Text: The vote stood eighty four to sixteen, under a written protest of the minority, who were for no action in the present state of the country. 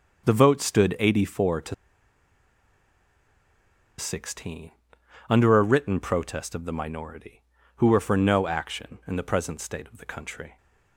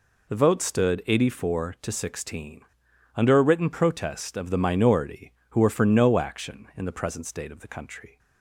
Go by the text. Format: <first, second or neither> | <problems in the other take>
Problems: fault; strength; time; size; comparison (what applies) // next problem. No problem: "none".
second | starts louder than the rest; until 1.3 s; 6.5 dB // pauses between "to" and "sixteen"; strong; at 1.7 s; 2.2 s long